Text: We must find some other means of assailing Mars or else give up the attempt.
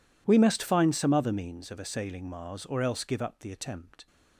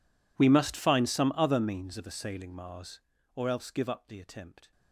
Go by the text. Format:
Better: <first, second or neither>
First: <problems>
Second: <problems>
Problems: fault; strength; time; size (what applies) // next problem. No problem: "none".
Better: first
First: none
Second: gets quieter; strong; throughout; 27.5 dB